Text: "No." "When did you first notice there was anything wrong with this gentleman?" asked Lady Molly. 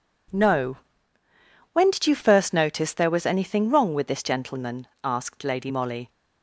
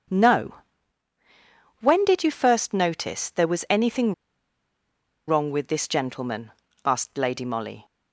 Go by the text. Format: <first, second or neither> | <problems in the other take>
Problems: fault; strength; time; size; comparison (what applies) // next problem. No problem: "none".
first | starts louder than the rest; until 2.3 s; 7 dB // pauses between "anything" and "wrong"; at 4.1 s; 1.1 s long